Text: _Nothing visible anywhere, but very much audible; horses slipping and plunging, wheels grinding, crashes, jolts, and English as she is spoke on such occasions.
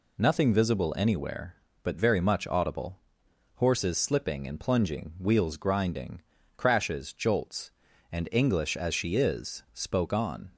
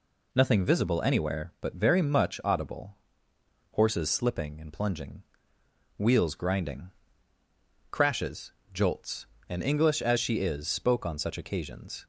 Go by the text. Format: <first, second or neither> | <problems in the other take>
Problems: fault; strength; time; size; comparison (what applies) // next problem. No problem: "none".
second | stops before "such occasions"; at 10.5 s